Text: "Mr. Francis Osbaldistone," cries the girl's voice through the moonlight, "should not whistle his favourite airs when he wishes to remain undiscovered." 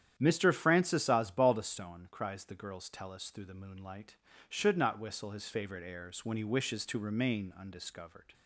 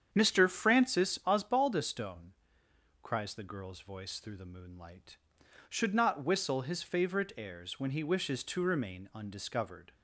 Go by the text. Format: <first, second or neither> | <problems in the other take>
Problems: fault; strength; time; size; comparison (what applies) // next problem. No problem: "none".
second | starts louder than the rest; strong; until 1.1 s; 9.5 dB; strong in the second // says "tellus" for "voice"; at 2.8 s